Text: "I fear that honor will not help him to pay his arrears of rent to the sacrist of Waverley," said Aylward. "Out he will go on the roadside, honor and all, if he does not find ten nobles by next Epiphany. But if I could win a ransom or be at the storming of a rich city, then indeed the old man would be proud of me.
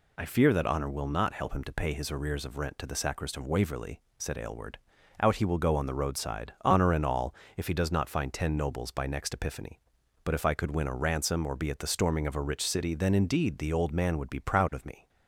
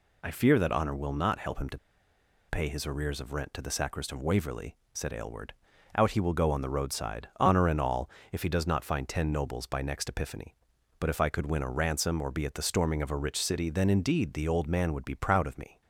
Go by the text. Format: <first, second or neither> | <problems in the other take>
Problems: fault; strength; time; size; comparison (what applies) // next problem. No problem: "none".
first | pauses between "to" and "pay"; noticeable; at 1.7 s; 0.71 s long